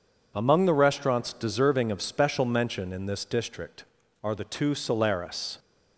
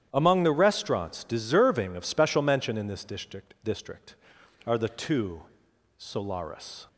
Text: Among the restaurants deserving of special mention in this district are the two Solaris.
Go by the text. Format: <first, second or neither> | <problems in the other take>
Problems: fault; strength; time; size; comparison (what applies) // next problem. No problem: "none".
first | starts louder than the rest; strong; until 1.1 s; 10.5 dB // says "district" twice; at 3.6 s // pauses between "two" and "Solaris"; noticeable; at 5.4 s; 0.56 s long